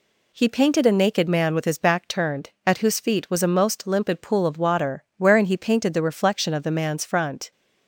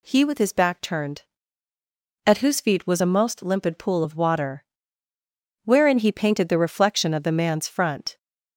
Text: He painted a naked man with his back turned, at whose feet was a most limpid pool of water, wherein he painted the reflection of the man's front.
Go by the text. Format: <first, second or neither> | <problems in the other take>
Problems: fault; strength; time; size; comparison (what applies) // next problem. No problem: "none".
first | skips "painted a naked man"; at 0.2 s